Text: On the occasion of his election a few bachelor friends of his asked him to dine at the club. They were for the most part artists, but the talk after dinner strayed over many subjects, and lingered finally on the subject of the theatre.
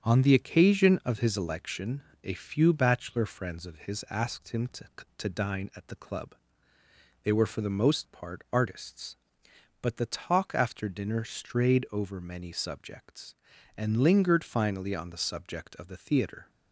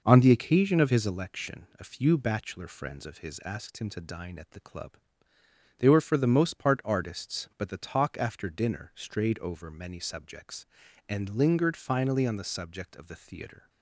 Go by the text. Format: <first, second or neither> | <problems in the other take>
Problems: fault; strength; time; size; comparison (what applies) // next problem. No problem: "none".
second | starts louder than the rest; until 1.0 s; 6.5 dB // pauses between "election" and "a"; slight; at 2.0 s; 0.22 s long // says "to" twice; at 5.1 s